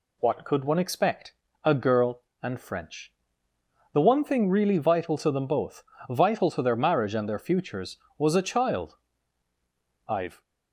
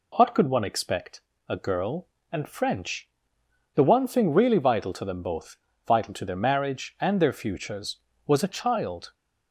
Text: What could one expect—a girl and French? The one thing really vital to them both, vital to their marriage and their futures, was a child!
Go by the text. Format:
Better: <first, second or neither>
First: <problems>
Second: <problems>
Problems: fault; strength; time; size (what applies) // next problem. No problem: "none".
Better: second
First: goes on to say "I've"; slight; from 10.0 s on; 0.34 s long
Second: none